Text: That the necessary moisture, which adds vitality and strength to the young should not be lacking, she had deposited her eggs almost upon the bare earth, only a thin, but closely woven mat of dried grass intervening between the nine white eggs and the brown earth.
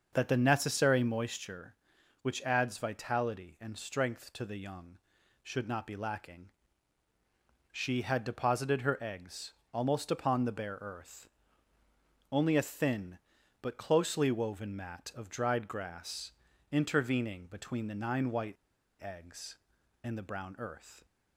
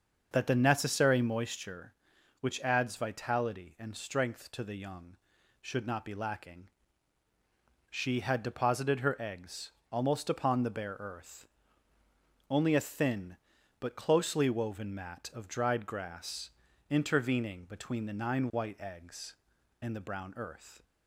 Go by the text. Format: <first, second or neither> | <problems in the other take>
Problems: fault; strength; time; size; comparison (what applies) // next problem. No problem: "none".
second | starts louder than the rest; until 1.1 s; 6.5 dB; also in the second // pauses between "eggs" and "almost"; slight; at 9.5 s; 0.20 s long; slight in the second // pauses between "grass" and "intervening"; at 16.2 s; 0.40 s long; also in the second // pauses between "white" and "eggs"; noticeable; at 18.5 s; 0.47 s long